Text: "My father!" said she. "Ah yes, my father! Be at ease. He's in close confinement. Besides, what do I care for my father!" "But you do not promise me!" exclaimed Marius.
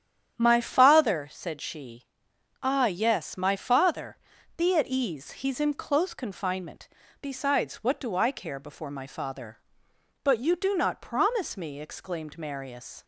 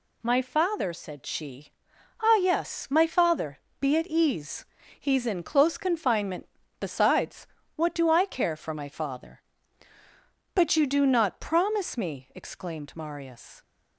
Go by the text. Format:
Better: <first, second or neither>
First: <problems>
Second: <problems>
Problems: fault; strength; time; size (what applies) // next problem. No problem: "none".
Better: second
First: starts louder than the rest; strong; until 1.4 s; 9 dB // says "before" for "for"; at 8.5 s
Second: none